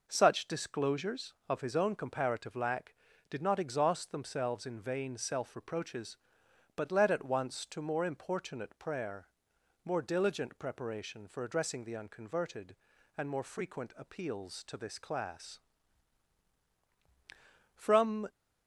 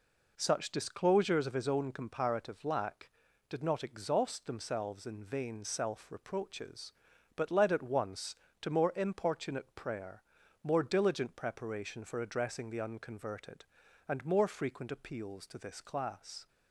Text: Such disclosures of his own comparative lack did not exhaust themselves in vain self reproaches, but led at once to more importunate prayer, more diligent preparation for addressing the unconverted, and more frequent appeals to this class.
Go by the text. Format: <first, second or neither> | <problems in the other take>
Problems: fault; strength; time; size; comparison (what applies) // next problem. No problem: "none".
second | goes on to say "From"; from 17.7 s on; 0.54 s long